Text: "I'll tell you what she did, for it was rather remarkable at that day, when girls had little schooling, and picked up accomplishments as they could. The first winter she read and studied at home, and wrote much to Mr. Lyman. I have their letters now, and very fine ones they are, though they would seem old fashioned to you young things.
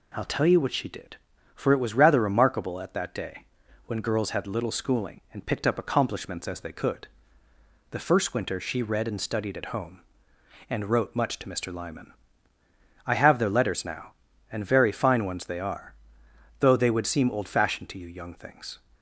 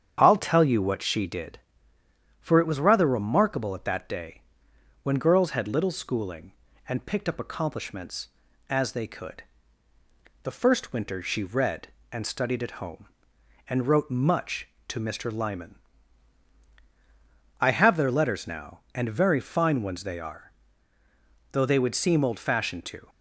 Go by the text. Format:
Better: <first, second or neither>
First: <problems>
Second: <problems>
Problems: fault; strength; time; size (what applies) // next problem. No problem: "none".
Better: first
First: none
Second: starts louder than the rest; strong; until 1.2 s; 8.5 dB // stops before "you young things"; at 23.0 s